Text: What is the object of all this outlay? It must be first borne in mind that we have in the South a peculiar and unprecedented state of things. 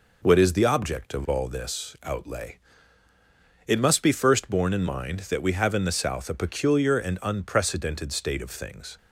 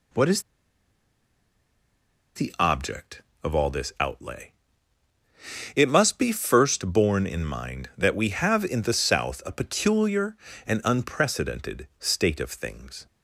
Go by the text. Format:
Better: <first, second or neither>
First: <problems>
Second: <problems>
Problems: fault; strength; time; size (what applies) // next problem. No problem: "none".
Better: first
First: none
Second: pauses between "is" and "the"; strong; at 0.4 s; 1.9 s long